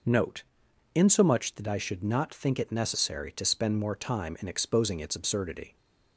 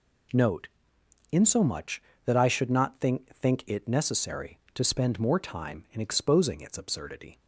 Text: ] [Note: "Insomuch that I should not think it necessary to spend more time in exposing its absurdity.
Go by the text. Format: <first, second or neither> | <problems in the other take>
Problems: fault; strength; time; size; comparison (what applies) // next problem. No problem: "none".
first | says "think" twice; at 3.3 s